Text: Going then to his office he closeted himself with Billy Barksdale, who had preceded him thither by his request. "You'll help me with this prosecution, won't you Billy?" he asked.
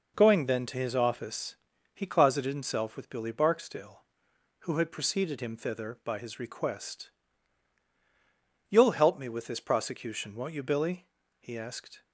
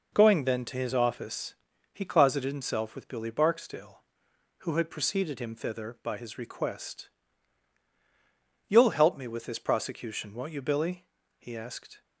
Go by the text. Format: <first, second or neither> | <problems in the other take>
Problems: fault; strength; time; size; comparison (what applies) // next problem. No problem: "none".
neither | pauses between "office" and "he"; the same in both